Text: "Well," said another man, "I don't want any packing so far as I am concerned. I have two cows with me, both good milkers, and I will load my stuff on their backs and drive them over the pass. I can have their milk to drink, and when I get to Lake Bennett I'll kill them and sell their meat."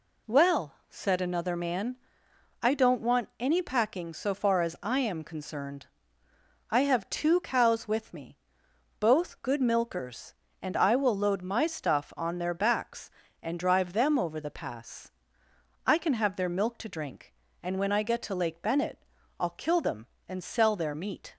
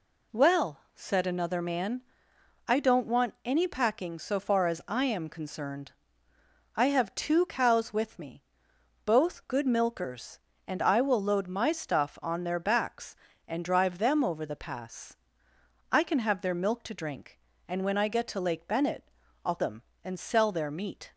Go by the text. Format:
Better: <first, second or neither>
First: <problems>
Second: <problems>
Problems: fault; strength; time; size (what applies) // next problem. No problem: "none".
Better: first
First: pauses between "Bennett" and "I'll"; slight; at 19.0 s; 0.34 s long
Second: pauses between "Bennett" and "I'll"; slight; at 19.0 s; 0.34 s long // skips "kill"; at 19.5 s